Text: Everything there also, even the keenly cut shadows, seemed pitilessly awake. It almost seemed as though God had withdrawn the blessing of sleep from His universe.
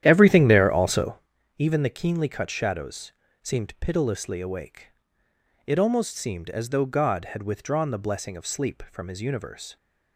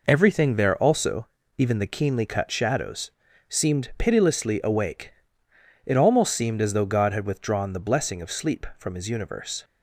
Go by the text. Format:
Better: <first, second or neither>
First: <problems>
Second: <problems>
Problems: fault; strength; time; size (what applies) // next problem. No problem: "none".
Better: second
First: starts louder than the rest; strong; until 1.3 s; 11 dB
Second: none